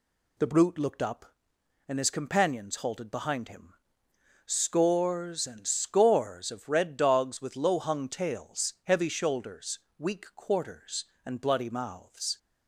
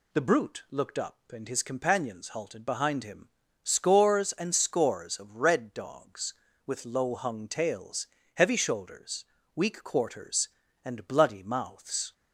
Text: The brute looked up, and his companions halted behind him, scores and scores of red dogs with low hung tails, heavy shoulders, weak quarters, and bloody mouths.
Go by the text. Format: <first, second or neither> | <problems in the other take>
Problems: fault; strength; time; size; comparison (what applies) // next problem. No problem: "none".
neither | none